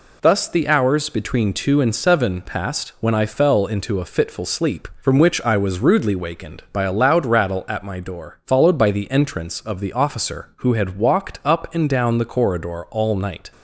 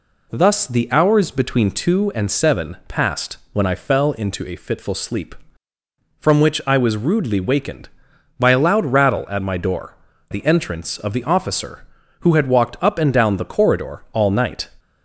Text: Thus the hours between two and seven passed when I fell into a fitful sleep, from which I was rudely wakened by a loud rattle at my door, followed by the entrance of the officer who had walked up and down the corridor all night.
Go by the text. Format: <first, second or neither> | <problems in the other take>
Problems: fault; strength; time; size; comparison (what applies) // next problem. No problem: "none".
first | pauses between "passed" and "when"; slight; at 3.3 s; 0.16 s long // skips "followed by"; at 10.1 s